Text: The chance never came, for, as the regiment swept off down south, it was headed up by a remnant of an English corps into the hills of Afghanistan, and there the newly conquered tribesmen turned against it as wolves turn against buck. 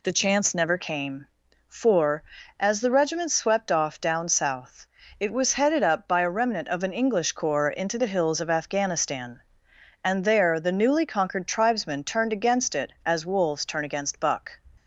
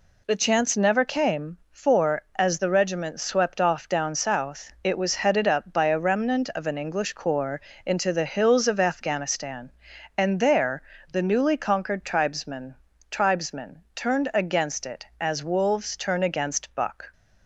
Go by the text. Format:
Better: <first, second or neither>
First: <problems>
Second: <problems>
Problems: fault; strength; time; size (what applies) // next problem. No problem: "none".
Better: first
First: none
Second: pauses between "corps" and "into"; slight; at 7.5 s; 0.24 s long // pauses between "there" and "the"; slight; at 10.7 s; 0.32 s long // says "tribesmen" twice; at 13.0 s